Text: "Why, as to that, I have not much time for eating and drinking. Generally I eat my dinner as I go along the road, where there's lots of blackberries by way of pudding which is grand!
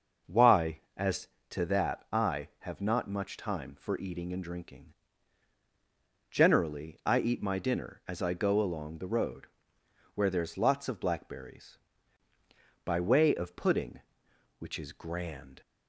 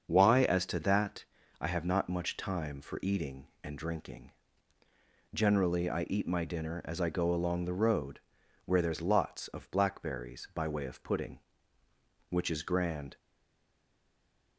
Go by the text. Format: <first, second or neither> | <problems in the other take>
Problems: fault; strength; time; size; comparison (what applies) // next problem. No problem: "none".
first | starts louder than the rest; until 1.1 s; 6.5 dB; noticeable in the first // stays silent after the last word; noticeable; from 13.1 s on; 1.4 s long